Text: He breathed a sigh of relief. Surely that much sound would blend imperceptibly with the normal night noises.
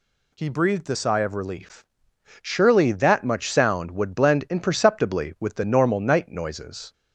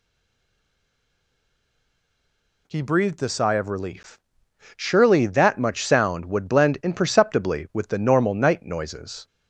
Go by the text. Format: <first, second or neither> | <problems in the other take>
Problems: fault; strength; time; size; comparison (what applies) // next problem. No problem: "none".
first | stays silent before the first word; strong; until 2.6 s; 2.6 s long